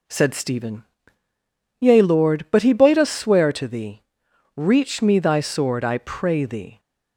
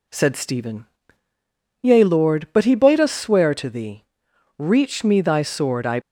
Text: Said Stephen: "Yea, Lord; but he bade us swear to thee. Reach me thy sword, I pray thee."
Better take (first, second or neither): first